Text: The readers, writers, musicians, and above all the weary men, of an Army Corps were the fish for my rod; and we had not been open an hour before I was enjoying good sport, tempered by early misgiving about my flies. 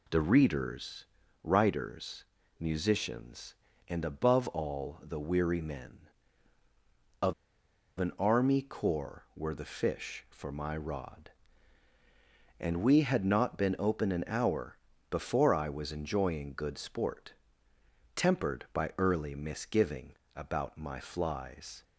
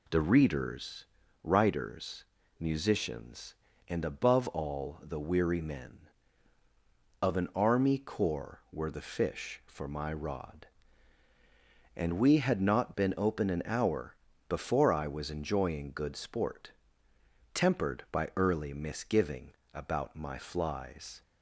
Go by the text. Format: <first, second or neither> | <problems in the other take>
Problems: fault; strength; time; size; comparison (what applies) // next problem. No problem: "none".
second | pauses between "of" and "an"; noticeable; at 7.3 s; 0.65 s long // pauses between "hour" and "before"; slight; at 14.7 s; 0.32 s long; slight in the second // pauses between "misgiving" and "about"; slight; at 20.1 s; 0.24 s long; slight in the second